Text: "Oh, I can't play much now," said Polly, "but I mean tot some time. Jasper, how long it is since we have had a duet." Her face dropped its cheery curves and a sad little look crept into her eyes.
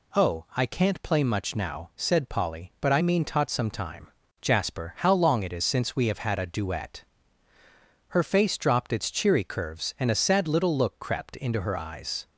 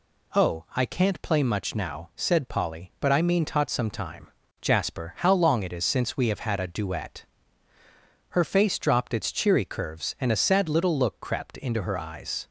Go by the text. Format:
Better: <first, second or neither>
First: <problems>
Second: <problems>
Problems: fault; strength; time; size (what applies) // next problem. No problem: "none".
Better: neither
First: none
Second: none